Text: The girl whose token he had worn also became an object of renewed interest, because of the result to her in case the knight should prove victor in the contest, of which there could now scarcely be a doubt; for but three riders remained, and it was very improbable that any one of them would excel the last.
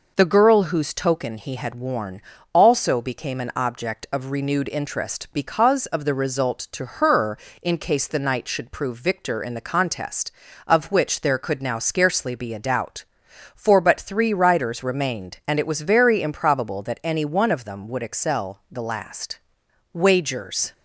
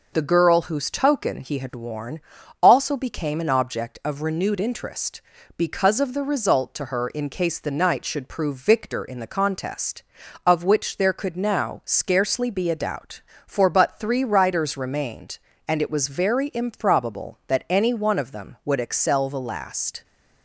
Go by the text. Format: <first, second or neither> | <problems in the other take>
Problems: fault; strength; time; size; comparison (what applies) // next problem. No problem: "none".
second | pauses between "worn" and "also"; slight; at 2.1 s; 0.32 s long; also in the second // goes on to say "Wagers"; noticeable; from 19.9 s on; 0.80 s long